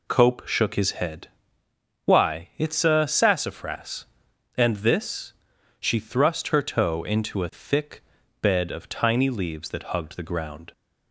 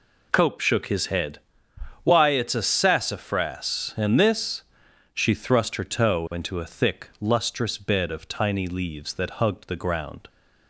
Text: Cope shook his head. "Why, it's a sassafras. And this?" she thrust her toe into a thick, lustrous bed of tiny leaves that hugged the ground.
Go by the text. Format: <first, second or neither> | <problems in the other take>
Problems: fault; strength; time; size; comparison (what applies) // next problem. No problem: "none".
second | skips "lustrous"; at 8.2 s